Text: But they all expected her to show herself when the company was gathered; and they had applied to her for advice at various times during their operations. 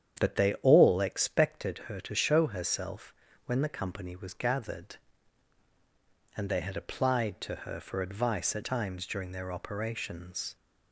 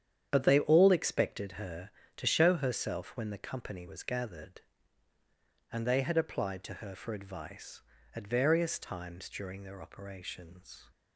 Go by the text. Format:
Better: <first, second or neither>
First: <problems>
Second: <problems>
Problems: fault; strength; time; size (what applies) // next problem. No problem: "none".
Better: second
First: starts louder than the rest; strong; until 1.2 s; 8.5 dB // pauses between "herself" and "when"; slight; at 3.1 s; 0.32 s long // skips "various"; at 8.6 s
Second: starts louder than the rest; strong; until 1.3 s; 9 dB